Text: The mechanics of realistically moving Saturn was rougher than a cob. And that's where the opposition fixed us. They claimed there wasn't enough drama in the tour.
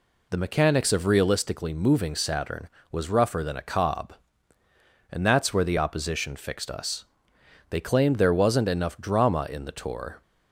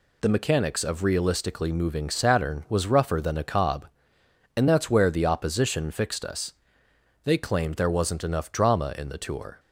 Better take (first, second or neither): second